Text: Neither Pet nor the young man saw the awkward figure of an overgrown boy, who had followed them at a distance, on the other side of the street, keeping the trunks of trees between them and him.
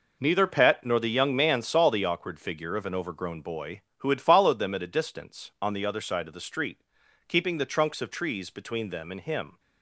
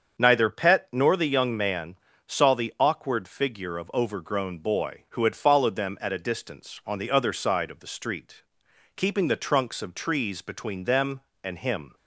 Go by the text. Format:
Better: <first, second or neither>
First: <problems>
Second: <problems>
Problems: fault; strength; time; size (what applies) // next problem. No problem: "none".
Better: first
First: none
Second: starts louder than the rest; until 1.2 s; 7 dB // pauses between "man" and "saw"; slight; at 1.9 s; 0.30 s long // skips "an"; at 3.9 s